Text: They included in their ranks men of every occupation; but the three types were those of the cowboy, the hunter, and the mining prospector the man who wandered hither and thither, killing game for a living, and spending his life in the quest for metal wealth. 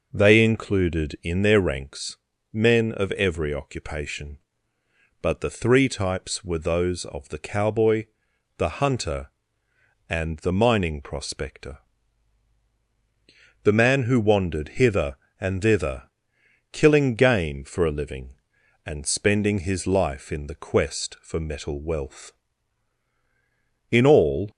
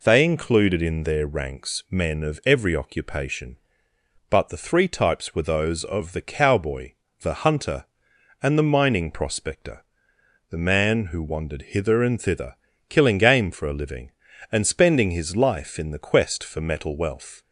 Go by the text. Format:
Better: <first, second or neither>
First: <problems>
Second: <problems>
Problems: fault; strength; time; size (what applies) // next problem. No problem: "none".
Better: second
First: pauses between "ranks" and "men"; slight; at 2.1 s; 0.34 s long // pauses between "prospector" and "the"; strong; at 11.7 s; 1.8 s long // goes on to say "In all"; from 23.9 s on; 0.58 s long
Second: pauses between "prospector" and "the"; noticeable; at 9.8 s; 0.66 s long